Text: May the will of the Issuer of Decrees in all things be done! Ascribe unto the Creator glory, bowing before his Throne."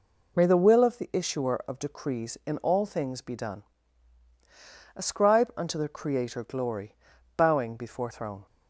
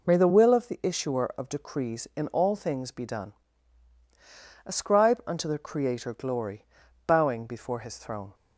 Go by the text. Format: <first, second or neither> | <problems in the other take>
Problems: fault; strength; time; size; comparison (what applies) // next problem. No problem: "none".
second | skips "his"; at 8.0 s